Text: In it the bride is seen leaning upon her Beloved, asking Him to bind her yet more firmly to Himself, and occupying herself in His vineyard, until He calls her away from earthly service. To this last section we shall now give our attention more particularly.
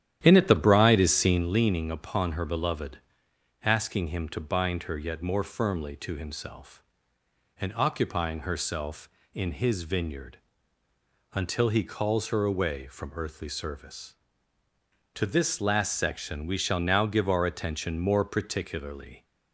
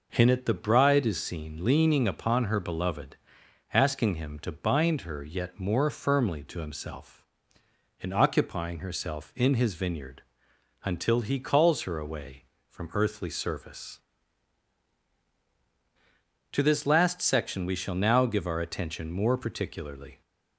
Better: second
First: starts louder than the rest; strong; until 1.5 s; 11 dB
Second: none

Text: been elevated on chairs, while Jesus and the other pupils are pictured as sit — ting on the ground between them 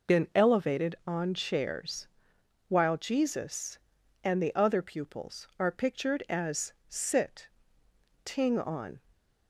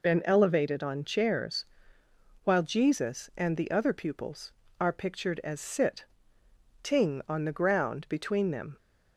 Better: second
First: stops before "the ground between them"; at 9.1 s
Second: none

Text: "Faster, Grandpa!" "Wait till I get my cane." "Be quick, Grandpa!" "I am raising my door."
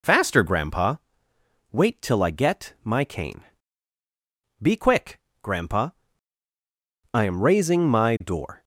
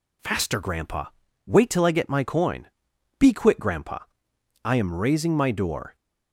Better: first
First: none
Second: says "coin" for "cane"; at 2.2 s

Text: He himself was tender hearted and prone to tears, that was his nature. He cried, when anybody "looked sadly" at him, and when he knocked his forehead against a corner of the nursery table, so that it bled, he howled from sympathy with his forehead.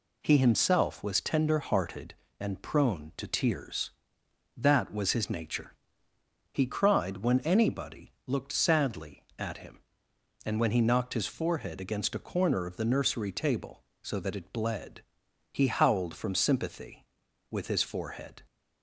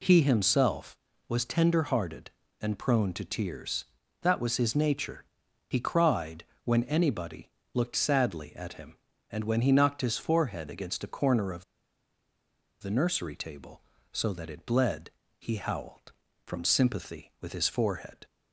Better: first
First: pauses between "anybody" and "looked"; slight; at 8.1 s; 0.16 s long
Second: pauses between "anybody" and "looked"; slight; at 7.5 s; 0.22 s long // pauses between "of" and "the"; at 11.6 s; 1.1 s long

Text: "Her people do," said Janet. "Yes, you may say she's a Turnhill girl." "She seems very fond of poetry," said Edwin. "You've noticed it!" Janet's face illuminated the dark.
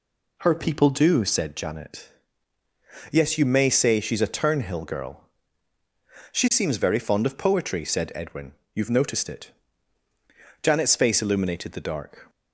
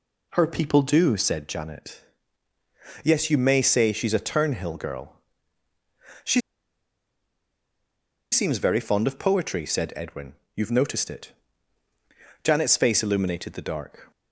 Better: first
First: none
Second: pauses between "She" and "seems"; strong; at 6.3 s; 1.9 s long

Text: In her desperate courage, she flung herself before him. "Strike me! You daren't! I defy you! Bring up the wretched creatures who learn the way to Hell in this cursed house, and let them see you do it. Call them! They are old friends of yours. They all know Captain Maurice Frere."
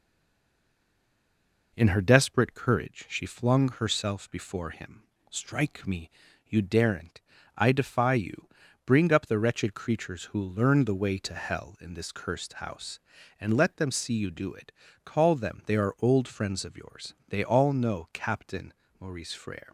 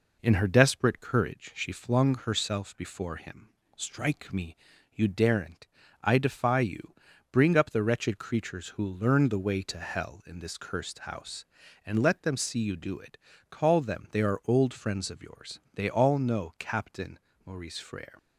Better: second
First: stays silent before the first word; noticeable; until 1.7 s; 1.7 s long // pauses between "Captain" and "Maurice"; slight; at 18.7 s; 0.26 s long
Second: pauses between "Captain" and "Maurice"; slight; at 17.1 s; 0.26 s long

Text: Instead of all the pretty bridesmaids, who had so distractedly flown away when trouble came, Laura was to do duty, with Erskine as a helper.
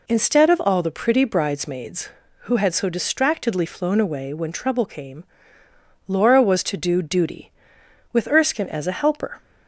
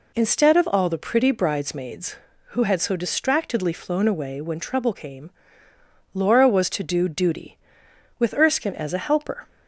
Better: neither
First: none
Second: none

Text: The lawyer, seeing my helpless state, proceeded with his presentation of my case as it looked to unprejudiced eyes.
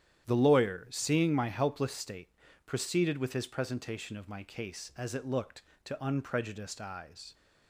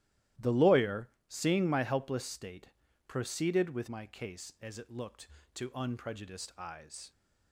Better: first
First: starts louder than the rest; strong; until 1.2 s; 10.5 dB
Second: starts louder than the rest; strong; until 1.5 s; 14.5 dB // skips "his presentation of"; at 3.8 s

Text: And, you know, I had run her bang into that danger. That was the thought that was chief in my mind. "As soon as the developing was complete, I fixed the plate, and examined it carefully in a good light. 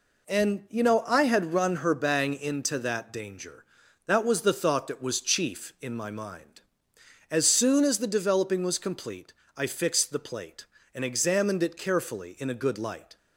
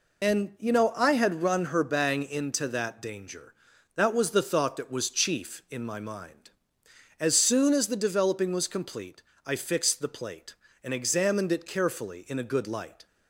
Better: first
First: none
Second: loses the start of "And"; at 0.2 s; 60 ms

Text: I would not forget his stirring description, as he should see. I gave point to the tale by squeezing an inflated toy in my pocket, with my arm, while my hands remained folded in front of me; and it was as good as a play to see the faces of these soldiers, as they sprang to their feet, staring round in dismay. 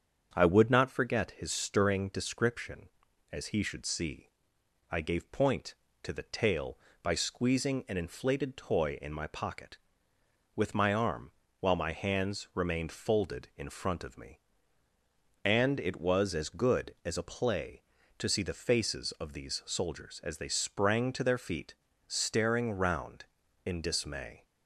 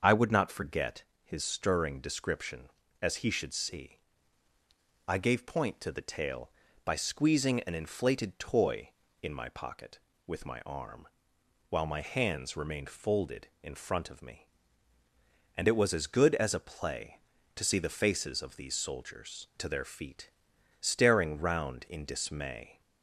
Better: first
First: starts louder than the rest; strong; until 1.3 s; 7 dB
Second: starts louder than the rest; until 1.0 s; 6.5 dB // pauses between "forget" and "his"; slight; at 1.0 s; 0.20 s long // skips "as they sprang"; at 19.5 s

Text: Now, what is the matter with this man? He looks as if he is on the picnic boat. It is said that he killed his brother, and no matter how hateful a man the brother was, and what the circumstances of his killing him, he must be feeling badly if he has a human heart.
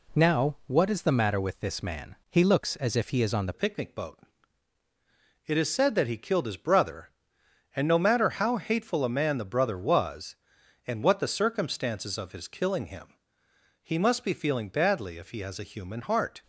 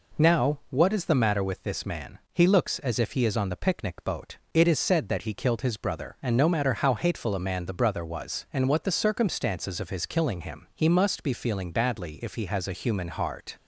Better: second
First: changes voice at "picnic"; from 3.5 s on; 12.9 s long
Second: none

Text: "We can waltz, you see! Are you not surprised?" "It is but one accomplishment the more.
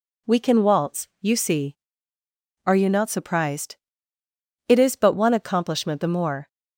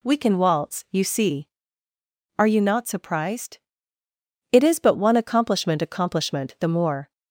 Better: first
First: none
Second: says "accomplishment" twice; at 5.7 s

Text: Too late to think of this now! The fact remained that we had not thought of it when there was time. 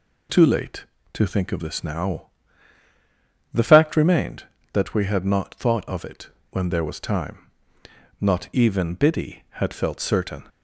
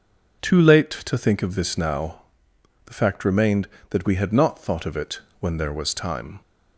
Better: second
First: pauses between "it" and "when"; slight; at 6.2 s; 0.24 s long // goes on to say "Not even Biddy had felt certain"; strong; from 8.2 s on; 2.2 s long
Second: pauses between "it" and "when"; slight; at 5.2 s; 0.18 s long

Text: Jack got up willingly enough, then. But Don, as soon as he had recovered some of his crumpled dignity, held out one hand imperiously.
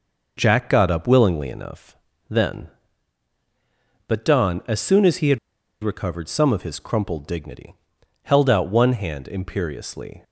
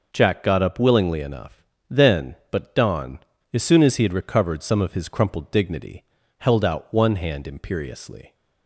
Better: second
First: pauses between "had" and "recovered"; at 5.3 s; 0.44 s long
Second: none

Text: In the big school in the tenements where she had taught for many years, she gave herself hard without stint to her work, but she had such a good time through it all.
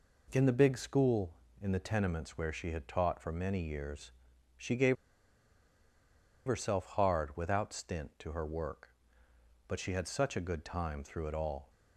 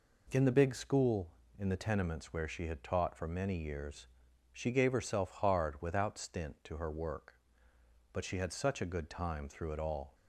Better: second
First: pauses between "gave" and "herself"; strong; at 4.9 s; 1.5 s long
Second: none

